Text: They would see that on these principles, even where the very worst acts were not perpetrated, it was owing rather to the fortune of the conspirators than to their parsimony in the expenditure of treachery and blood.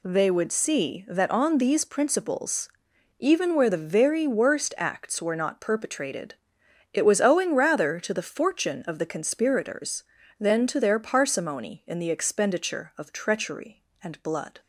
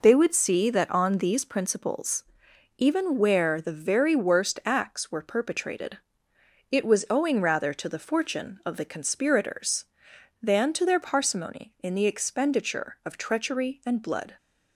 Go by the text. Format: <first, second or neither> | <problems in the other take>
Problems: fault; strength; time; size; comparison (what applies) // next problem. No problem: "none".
first | skips "not"; at 5.2 s